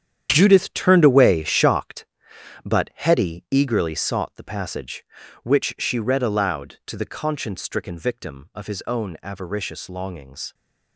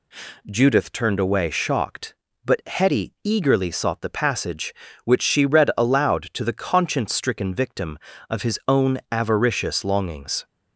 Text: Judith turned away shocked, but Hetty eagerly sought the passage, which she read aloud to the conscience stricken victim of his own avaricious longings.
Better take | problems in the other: second | gets quieter; strong; throughout; 11.5 dB

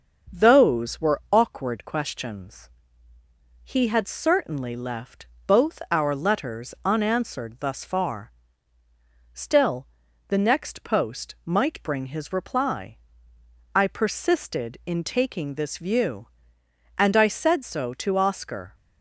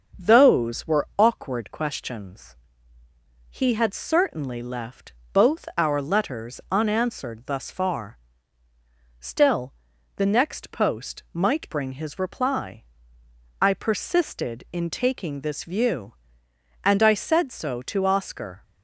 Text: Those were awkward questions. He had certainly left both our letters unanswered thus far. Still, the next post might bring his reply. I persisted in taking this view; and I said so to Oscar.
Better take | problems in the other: neither | starts louder than the rest; the same in both // pauses between "left" and "both"; slight; the same in both

